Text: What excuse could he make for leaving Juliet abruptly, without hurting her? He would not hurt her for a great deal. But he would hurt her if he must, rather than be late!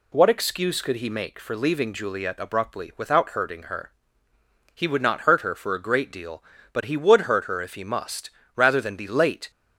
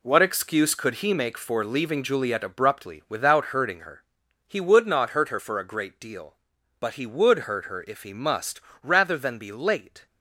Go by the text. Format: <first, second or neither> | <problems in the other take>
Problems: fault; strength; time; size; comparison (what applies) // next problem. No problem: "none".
first | gets quieter; strong; throughout; 9 dB